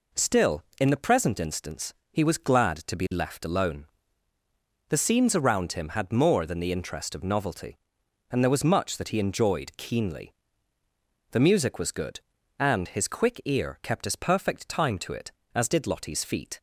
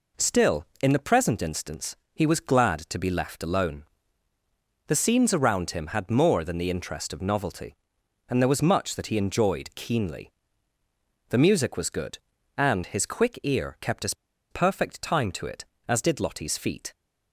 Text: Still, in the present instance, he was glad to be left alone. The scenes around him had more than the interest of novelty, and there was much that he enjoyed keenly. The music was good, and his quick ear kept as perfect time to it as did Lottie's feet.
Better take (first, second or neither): first